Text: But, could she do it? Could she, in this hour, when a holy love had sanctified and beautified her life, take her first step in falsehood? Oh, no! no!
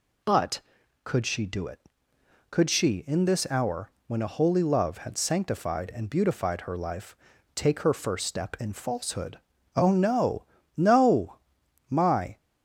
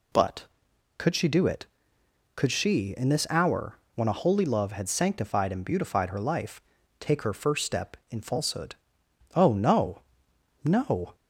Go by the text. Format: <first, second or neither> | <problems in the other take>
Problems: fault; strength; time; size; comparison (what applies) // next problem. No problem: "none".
second | goes on to say "My"; slight; from 11.8 s on; 0.48 s long